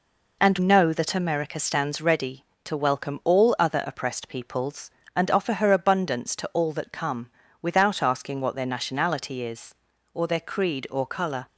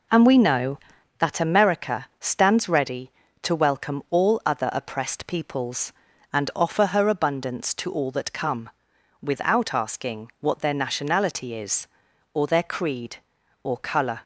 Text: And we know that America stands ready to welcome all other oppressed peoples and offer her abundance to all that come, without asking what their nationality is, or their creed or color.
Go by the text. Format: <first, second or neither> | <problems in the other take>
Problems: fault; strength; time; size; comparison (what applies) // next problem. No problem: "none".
second | skips "we"; at 0.5 s